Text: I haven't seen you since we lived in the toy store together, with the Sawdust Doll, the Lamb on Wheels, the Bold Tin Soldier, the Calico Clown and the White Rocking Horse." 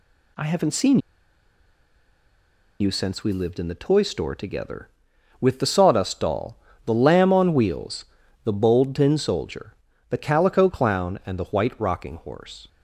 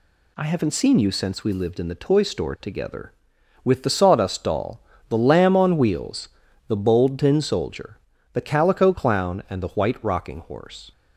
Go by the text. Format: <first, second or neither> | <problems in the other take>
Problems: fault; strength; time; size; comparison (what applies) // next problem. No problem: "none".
second | pauses between "seen" and "you"; strong; at 0.9 s; 1.8 s long